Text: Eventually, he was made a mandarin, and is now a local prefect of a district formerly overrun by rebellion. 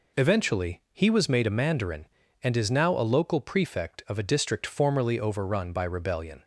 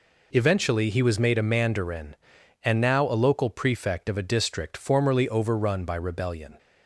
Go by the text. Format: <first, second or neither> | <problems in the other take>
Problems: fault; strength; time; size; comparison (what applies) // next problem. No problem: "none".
first | skips "is"; at 2.7 s